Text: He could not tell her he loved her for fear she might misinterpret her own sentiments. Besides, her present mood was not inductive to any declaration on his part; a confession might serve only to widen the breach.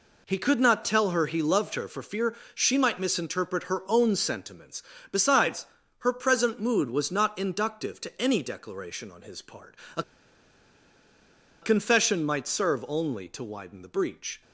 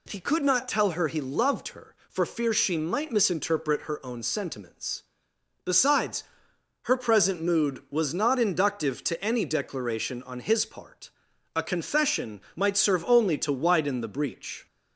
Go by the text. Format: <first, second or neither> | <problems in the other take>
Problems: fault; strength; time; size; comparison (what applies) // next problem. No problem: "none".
second | pauses between "fear" and "she"; slight; at 2.3 s; 0.20 s long // pauses between "a" and "confession"; strong; at 10.0 s; 1.6 s long